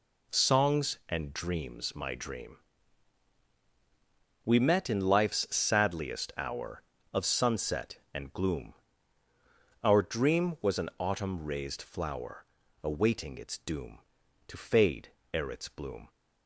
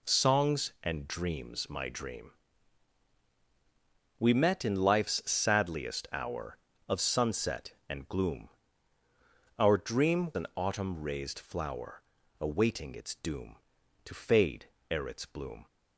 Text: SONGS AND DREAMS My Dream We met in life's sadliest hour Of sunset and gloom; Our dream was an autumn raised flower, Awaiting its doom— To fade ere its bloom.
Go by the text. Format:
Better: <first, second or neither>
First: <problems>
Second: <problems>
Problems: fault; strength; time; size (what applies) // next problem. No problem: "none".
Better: first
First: pauses between "Dream" and "We"; strong; at 2.5 s; 1.8 s long // pauses between "fade" and "ere"; slight; at 15.0 s; 0.24 s long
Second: pauses between "Dream" and "We"; strong; at 2.3 s; 1.8 s long // skips "was"; at 10.3 s // pauses between "fade" and "ere"; slight; at 14.6 s; 0.24 s long